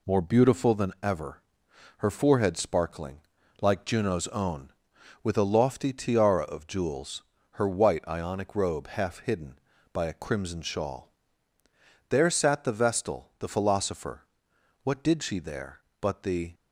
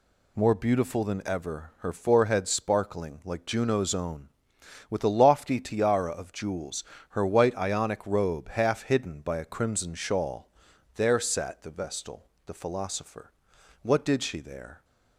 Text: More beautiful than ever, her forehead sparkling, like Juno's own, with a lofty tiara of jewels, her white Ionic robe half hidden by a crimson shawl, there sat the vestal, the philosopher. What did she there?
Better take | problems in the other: second | goes on to say "But the"; from 16.0 s on; 0.52 s long

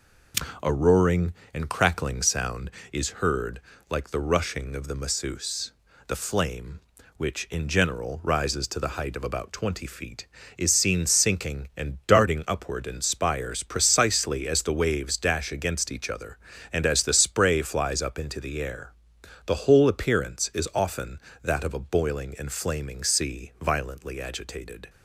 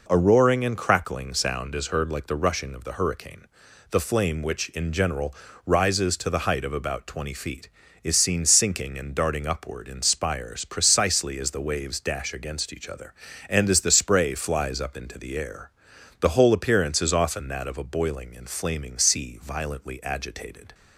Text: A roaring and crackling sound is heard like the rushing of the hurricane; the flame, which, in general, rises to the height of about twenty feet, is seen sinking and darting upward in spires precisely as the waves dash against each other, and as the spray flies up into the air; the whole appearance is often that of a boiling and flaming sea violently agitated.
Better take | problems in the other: second | pauses between "heard" and "like"; slight; at 3.6 s; 0.28 s long // says "masseuse" for "hurricane"; at 4.9 s

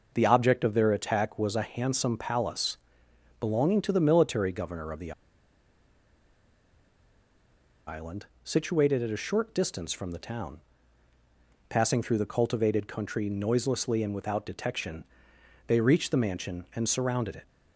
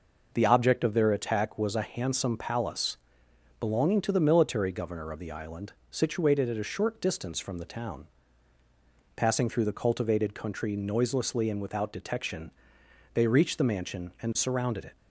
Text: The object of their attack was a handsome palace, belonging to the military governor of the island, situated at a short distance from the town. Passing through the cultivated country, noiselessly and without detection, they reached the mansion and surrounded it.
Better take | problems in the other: second | pauses between "the" and "island"; strong; at 5.1 s; 2.7 s long

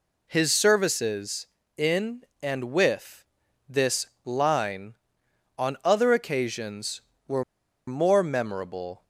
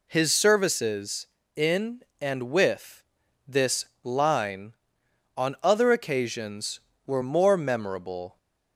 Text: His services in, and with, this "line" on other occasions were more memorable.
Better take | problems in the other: second | pauses between "this" and "line"; slight; at 4.0 s; 0.18 s long; slight in the second // pauses between "were" and "more"; at 7.4 s; 0.45 s long

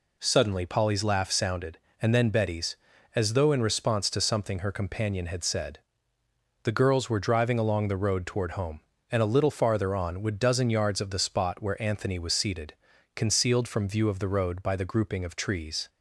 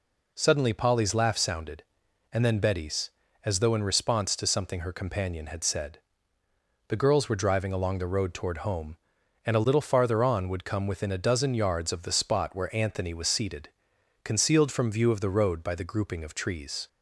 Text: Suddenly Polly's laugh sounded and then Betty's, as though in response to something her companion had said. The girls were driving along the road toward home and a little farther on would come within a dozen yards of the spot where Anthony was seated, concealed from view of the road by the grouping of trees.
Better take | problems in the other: second | skips "come within a"; at 10.3 s

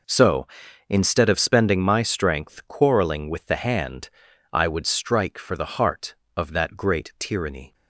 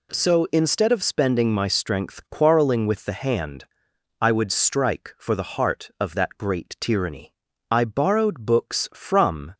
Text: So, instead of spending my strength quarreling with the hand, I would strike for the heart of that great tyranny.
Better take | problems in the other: first | goes on to say "I borrowed books from"; strong; from 7.7 s on; 1.8 s long

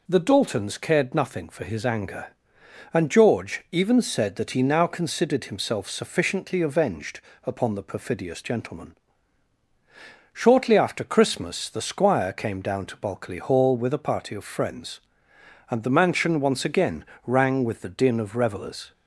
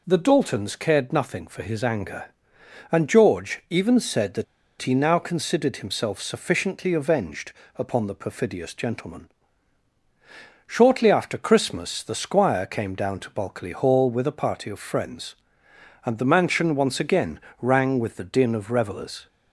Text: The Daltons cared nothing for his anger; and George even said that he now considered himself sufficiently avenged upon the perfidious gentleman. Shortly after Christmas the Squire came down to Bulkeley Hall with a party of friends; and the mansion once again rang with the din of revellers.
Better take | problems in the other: first | pauses between "that" and "he"; at 4.4 s; 0.36 s long // pauses between "avenged" and "upon"; slight; at 7.5 s; 0.24 s long; slight in the first // pauses between "again" and "rang"; slight; at 17.3 s; 0.22 s long; slight in the first

